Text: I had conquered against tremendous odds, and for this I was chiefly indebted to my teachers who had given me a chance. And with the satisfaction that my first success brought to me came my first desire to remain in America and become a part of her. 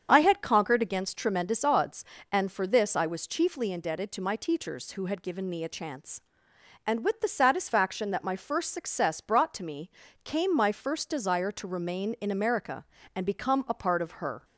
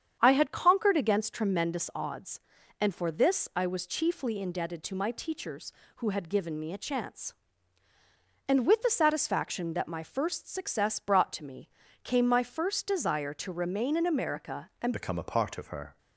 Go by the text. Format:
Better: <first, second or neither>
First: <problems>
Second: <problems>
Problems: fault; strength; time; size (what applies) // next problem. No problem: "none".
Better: first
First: starts louder than the rest; strong; until 1.1 s; 7.5 dB // pauses between "me" and "came"; slight; at 9.9 s; 0.34 s long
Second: starts louder than the rest; strong; until 1.2 s; 8.5 dB // pauses between "me" and "came"; slight; at 11.6 s; 0.34 s long // changes voice at "become"; from 14.9 s on; 1.0 s long